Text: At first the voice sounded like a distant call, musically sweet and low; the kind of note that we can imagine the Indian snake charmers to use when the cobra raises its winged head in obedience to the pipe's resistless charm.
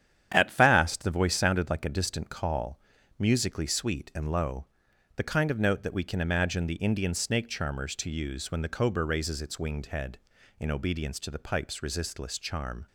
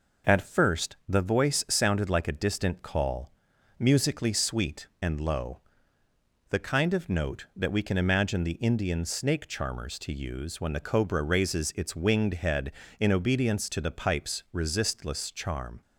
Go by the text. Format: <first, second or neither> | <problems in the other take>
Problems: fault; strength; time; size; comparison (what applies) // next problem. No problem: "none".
second | starts louder than the rest; strong; until 1.3 s; 9.5 dB // says "fast" for "first"; at 0.5 s